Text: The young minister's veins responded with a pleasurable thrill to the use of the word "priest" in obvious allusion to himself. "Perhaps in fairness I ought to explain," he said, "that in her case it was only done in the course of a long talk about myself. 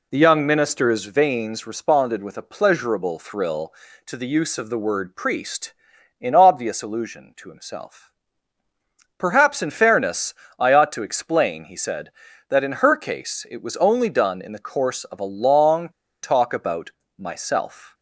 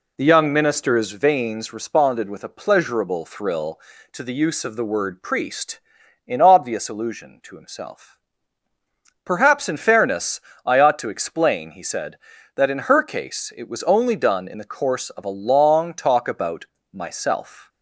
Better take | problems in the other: second | pauses between "fairness" and "I"; slight; at 10.3 s; 0.24 s long; slight in the second // pauses between "long" and "talk"; slight; at 15.8 s; 0.33 s long // pauses between "about" and "myself"; slight; at 16.9 s; 0.26 s long; slight in the second

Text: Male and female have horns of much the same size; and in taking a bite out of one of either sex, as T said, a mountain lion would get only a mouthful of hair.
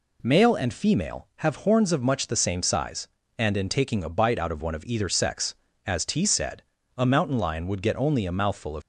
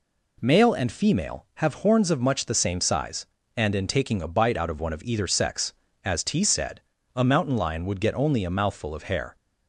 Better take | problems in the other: second | stops before "hair"; at 8.8 s

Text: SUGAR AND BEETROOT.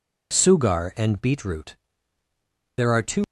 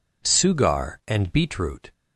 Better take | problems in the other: second | goes on to say "There are two"; slight; from 2.7 s on; 0.48 s long

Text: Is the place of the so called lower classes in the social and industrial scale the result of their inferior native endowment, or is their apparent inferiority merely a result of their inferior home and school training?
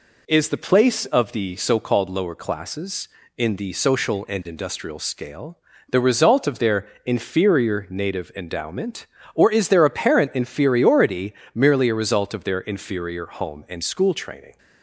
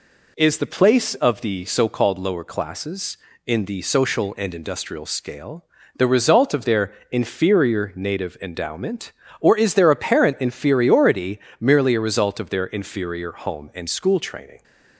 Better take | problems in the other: neither | pauses between "scale" and "the"; slight; the same in both // pauses between "their" and "inferior"; slight; the same in both // pauses between "inferiority" and "merely"; slight; the same in both

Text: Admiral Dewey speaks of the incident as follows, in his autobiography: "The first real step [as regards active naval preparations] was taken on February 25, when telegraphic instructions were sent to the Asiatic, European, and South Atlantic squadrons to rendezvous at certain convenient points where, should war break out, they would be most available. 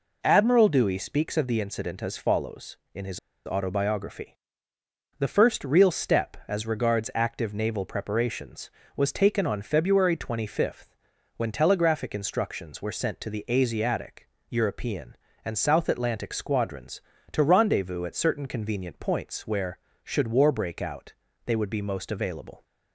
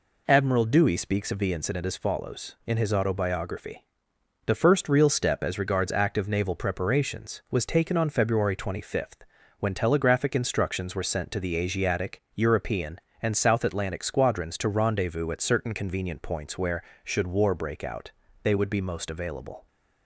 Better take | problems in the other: second | pauses between "his" and "autobiography"; slight; at 3.1 s; 0.26 s long

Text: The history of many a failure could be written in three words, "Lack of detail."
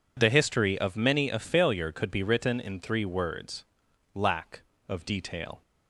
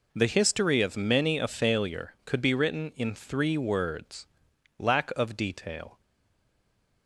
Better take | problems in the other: first | stays silent after the last word; from 6.0 s on; 1.0 s long

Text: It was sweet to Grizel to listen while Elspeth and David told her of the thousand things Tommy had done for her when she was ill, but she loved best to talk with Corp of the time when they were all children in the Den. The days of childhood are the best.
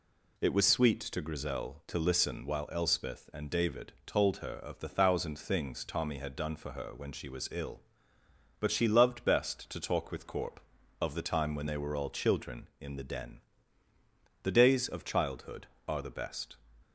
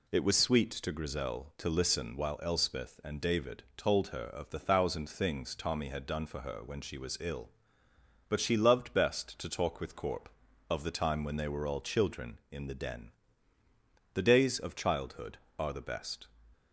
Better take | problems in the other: neither | none

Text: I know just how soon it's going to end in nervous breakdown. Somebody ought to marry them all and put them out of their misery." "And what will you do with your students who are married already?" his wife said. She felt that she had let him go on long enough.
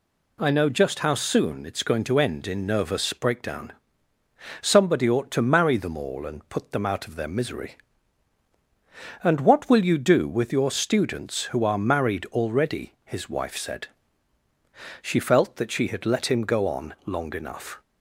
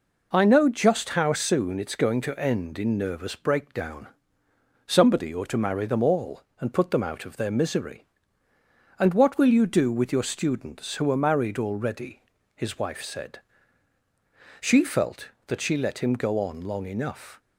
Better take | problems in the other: first | skips "had"; at 15.7 s

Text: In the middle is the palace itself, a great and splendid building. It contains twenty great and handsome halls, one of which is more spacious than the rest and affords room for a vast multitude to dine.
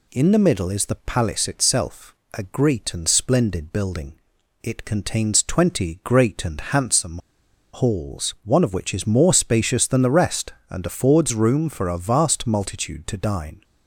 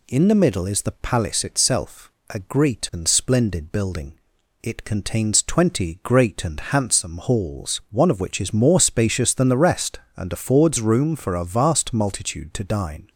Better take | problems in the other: second | pauses between "handsome" and "halls"; noticeable; at 7.1 s; 0.55 s long

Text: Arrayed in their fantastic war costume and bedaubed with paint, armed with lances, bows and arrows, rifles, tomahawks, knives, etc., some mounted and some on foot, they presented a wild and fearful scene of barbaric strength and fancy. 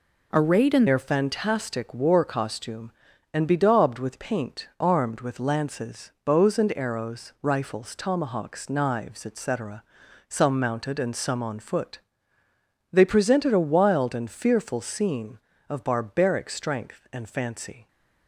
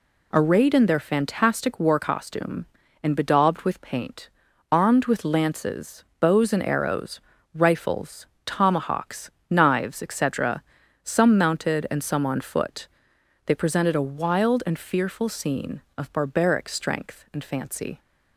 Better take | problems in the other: second | changes voice at "their"; from 0.8 s on; 17.0 s long

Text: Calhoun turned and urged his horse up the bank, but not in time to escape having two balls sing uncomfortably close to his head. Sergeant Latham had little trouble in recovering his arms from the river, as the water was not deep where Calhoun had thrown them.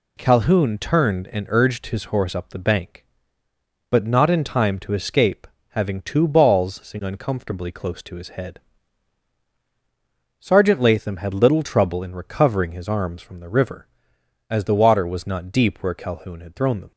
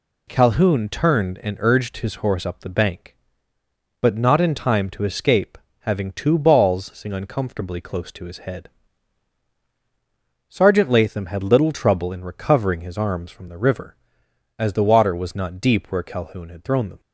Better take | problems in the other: neither | pauses between "escape" and "having"; slight; the same in both

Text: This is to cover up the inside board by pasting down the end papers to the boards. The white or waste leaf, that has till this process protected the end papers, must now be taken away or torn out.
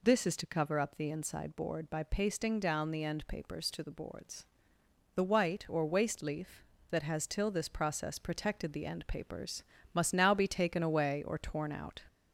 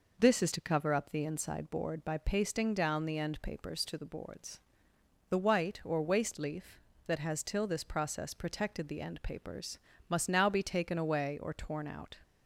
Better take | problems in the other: second | gets louder; slight; throughout; 2 dB

